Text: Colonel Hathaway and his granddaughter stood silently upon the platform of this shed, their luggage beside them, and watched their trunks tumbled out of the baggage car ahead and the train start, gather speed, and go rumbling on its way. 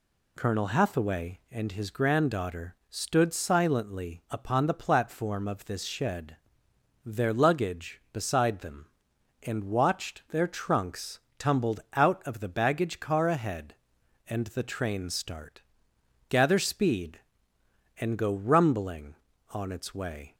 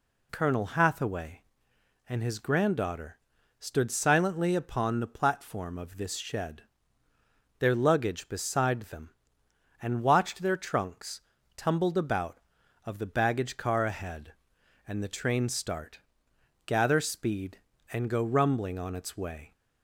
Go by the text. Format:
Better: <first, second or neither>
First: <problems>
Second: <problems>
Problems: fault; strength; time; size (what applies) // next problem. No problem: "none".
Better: first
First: pauses between "granddaughter" and "stood"; slight; at 2.7 s; 0.16 s long // pauses between "trunks" and "tumbled"; slight; at 11.2 s; 0.18 s long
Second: pauses between "granddaughter" and "stood"; at 3.1 s; 0.40 s long // pauses between "trunks" and "tumbled"; slight; at 11.2 s; 0.36 s long // says "about" for "out"; at 11.9 s